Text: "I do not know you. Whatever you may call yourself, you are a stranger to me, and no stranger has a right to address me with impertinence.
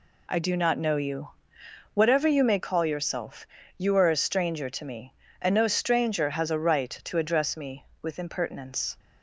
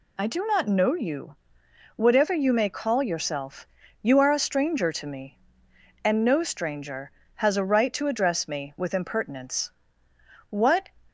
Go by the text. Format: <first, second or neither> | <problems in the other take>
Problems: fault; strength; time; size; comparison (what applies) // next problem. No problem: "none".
first | goes on to say "What"; slight; from 10.4 s on; 0.40 s long